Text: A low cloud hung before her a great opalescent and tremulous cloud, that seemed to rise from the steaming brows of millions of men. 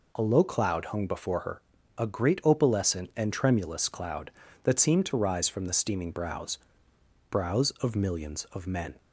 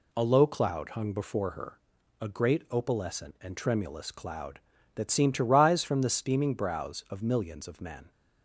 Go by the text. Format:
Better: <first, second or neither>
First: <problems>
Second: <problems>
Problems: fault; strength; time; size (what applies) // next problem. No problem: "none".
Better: second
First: pauses between "her" and "a"; at 1.6 s; 0.38 s long // says "brows" twice; at 7.2 s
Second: pauses between "her" and "a"; at 1.7 s; 0.42 s long